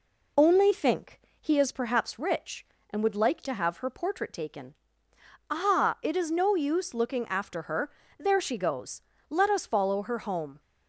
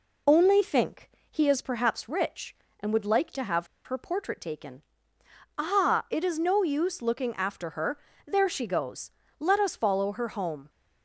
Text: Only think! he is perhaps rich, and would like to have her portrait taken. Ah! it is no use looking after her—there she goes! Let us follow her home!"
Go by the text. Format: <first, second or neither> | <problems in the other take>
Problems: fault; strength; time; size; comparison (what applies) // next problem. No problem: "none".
first | pauses between "have" and "her"; slight; at 3.6 s; 0.18 s long